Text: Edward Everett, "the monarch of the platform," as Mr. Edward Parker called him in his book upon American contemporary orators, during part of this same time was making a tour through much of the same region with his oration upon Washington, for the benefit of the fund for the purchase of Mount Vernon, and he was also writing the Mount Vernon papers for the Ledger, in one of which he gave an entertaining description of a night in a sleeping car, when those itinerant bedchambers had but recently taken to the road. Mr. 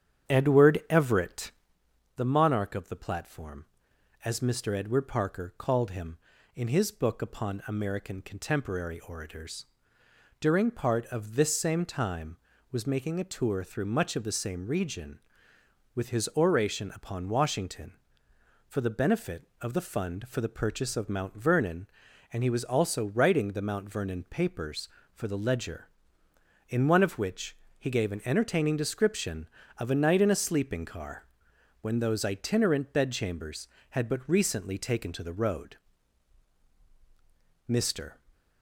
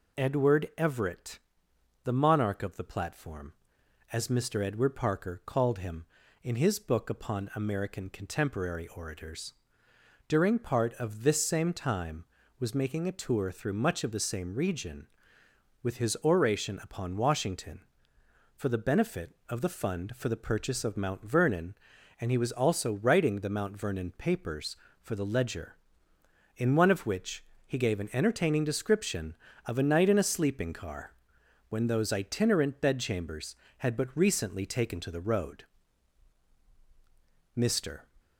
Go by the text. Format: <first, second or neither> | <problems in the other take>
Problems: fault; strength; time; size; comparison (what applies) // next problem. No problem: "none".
second | starts louder than the rest; strong; until 1.8 s; 9 dB // pauses between "which" and "he"; slight; at 27.5 s; 0.22 s long; slight in the second